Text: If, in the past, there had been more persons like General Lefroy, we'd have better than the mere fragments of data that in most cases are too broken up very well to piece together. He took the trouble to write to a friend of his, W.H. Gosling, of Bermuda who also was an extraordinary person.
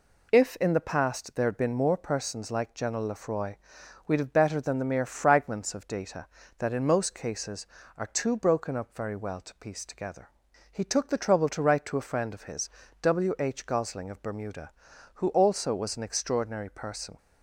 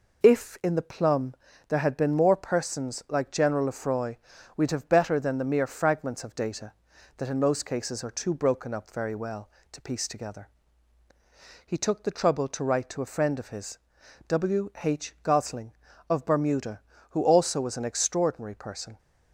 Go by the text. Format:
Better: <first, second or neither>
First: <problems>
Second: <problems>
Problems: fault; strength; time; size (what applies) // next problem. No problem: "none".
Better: first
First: none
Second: says "plum" for "past"; at 0.8 s